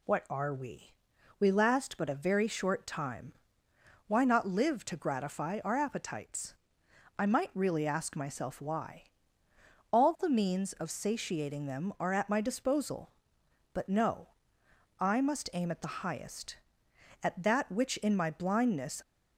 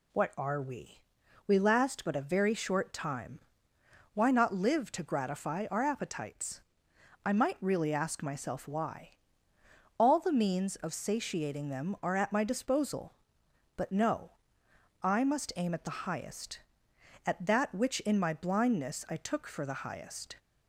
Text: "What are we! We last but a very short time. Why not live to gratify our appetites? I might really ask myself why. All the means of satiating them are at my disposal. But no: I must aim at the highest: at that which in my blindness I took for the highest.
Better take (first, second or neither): second